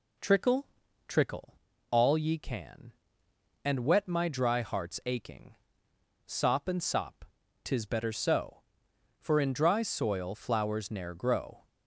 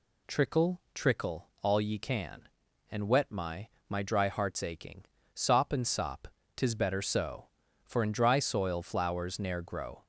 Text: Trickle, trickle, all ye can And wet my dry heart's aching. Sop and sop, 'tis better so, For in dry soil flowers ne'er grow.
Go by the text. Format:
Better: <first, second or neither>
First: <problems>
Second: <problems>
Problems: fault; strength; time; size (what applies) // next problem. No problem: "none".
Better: first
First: none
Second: says "my" twice; at 3.9 s